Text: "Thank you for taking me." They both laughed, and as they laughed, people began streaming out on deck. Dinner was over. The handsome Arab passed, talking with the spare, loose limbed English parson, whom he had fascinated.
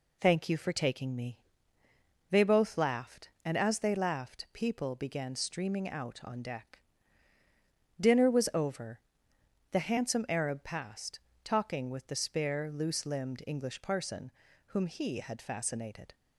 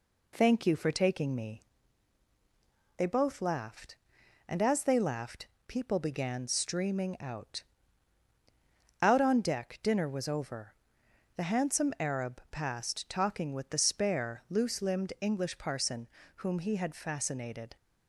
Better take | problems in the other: first | says "out" twice; at 9.0 s

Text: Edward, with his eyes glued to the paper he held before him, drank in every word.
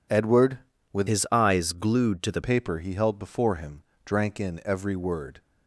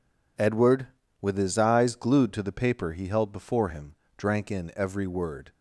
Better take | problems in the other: second | changes voice from "his" to "the"; from 1.0 to 2.3 s; 1.3 s long

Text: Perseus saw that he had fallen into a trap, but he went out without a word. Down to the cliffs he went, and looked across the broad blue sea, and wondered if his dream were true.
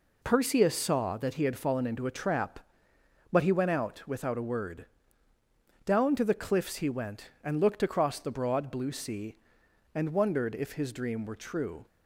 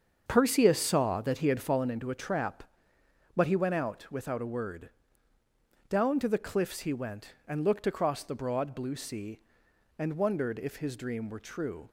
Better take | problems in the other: first | starts louder than the rest; until 1.9 s; 7 dB

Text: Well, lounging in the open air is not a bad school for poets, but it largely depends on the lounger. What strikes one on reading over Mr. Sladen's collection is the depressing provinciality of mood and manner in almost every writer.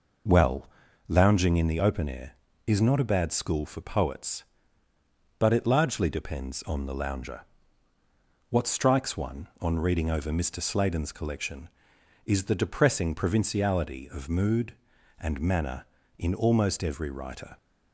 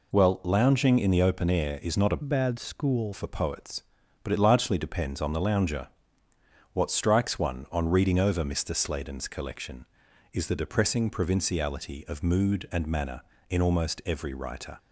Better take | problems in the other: first | changes voice from "bad" to "school"; from 2.2 to 3.1 s; 0.9 s long

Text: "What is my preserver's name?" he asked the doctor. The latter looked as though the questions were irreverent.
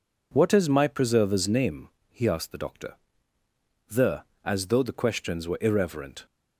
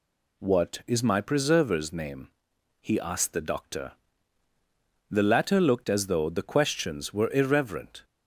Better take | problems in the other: second | skips "latter looked"; at 4.3 s

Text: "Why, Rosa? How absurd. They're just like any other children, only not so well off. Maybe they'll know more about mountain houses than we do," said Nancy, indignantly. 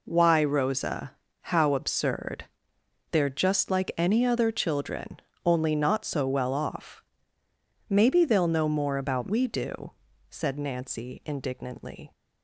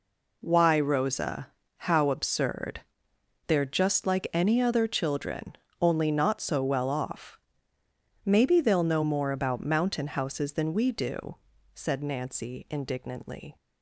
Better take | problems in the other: second | skips "mountain houses than"; at 9.2 s

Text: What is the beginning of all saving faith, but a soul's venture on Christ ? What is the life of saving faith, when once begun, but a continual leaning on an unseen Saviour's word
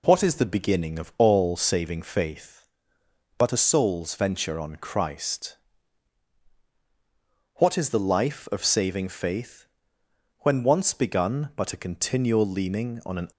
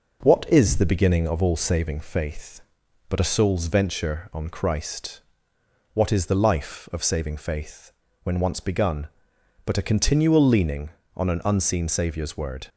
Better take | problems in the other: second | stops before "unseen Saviour's word"; at 13.3 s

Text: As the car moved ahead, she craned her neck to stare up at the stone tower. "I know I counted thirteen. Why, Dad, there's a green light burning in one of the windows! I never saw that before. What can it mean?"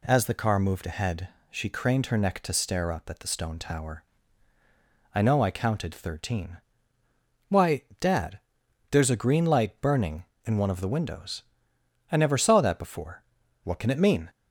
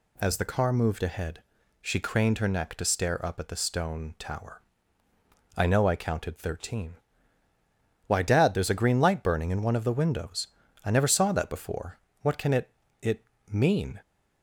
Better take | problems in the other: first | says "it" twice; at 13.0 s

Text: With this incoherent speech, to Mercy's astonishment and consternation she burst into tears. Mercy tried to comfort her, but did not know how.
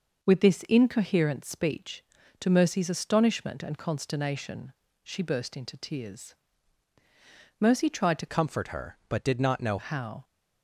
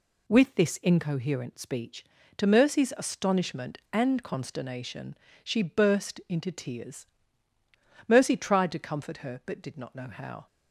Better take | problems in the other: second | pauses between "consternation" and "she"; slight; at 4.7 s; 0.32 s long; slight in the second // changes voice from "comfort" to "know"; from 8.2 to 9.7 s; 1.5 s long

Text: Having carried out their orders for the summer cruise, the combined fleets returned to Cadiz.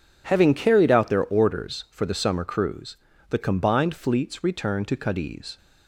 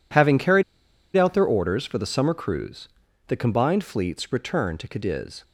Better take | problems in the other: first | pauses between "carried" and "out"; noticeable; at 0.6 s; 0.53 s long

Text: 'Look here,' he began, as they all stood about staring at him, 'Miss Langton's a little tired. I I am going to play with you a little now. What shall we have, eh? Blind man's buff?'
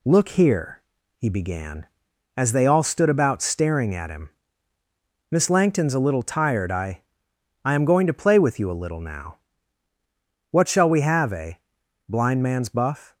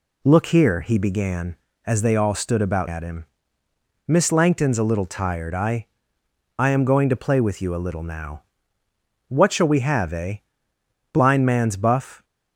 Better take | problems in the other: first | skips "staring"; at 2.8 s // pauses between "I" and "I"; noticeable; at 5.8 s; 0.72 s long; noticeable in the first

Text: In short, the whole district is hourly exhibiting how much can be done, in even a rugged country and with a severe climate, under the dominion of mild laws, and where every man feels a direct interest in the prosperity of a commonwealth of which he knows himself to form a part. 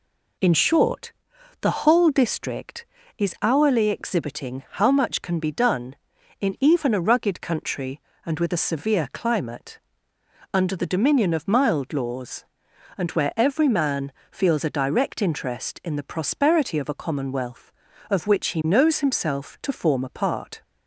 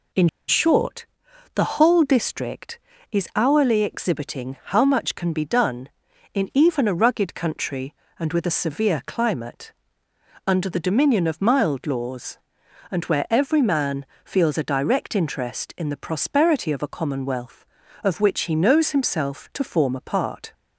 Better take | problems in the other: first | pauses between "In" and "short"; slight; at 0.2 s; 0.20 s long // pauses between "man" and "feels"; slight; at 14.0 s; 0.18 s long; slight in the first

